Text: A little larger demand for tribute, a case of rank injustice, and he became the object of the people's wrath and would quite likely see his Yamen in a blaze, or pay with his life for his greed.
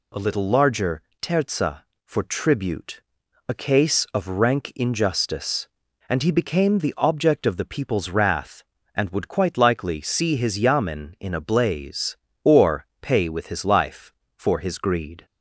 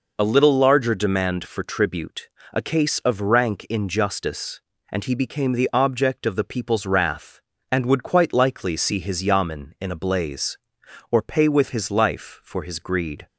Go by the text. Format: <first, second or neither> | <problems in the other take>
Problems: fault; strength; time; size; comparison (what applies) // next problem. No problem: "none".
second | says "terza" for "demand"; at 1.2 s // pauses between "or" and "pay"; slight; at 12.8 s; 0.16 s long